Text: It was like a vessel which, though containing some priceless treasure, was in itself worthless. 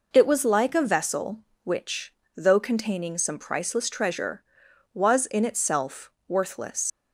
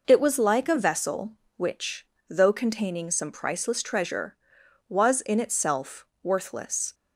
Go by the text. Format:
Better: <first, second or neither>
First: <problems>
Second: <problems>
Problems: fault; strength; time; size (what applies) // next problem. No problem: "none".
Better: second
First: pauses between "itself" and "worthless"; slight; at 6.0 s; 0.18 s long // leaves "worthless" unfinished; at 6.9 s; 90 ms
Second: pauses between "itself" and "worthless"; slight; at 6.0 s; 0.18 s long